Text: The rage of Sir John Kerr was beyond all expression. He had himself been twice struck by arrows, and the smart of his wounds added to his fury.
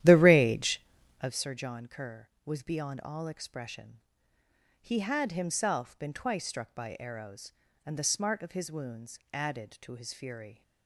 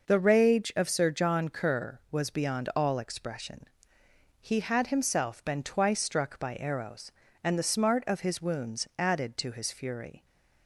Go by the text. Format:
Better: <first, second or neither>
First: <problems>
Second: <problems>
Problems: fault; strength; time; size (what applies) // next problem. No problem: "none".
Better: second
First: starts louder than the rest; strong; until 1.4 s; 12 dB // pauses between "wounds" and "added"; slight; at 9.1 s; 0.16 s long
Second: none